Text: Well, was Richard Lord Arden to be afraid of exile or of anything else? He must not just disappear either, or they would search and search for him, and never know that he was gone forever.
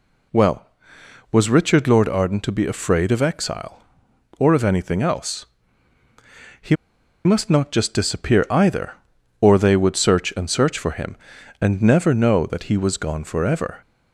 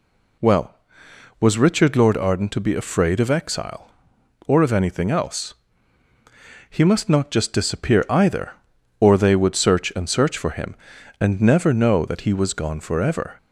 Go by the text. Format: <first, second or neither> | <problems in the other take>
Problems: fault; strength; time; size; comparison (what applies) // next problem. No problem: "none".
second | pauses between "He" and "must"; noticeable; at 6.7 s; 0.49 s long